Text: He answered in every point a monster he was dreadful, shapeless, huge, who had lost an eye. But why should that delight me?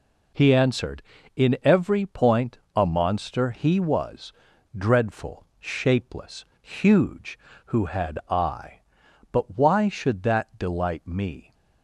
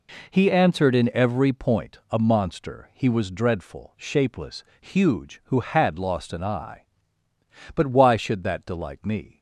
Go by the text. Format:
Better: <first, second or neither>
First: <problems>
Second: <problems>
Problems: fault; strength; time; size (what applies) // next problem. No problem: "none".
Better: second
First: pauses between "point" and "a"; slight; at 2.5 s; 0.18 s long // pauses between "was" and "dreadful"; at 4.3 s; 0.42 s long // skips "lost an"; at 8.2 s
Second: none